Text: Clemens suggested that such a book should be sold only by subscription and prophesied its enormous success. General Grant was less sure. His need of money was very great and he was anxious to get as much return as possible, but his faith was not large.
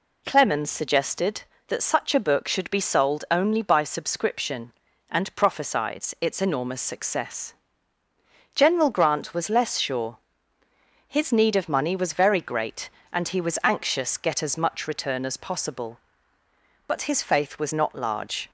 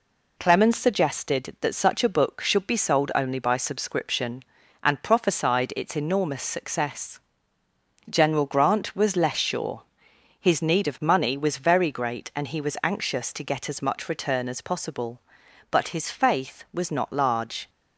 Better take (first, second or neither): second